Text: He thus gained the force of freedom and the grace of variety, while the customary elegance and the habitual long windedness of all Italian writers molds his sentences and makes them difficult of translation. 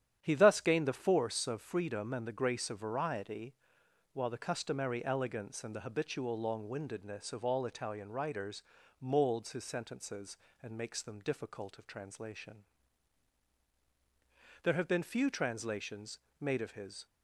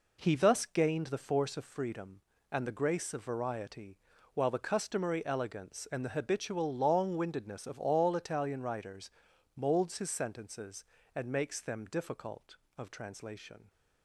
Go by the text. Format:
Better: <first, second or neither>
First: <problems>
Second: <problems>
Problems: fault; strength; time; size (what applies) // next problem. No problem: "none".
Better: second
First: starts louder than the rest; strong; until 1.2 s; 10 dB // pauses between "writers" and "molds"; at 8.6 s; 0.38 s long // goes on to say "There have been few translations made of his"; strong; from 14.6 s on; 2.4 s long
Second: pauses between "writers" and "molds"; noticeable; at 9.0 s; 0.46 s long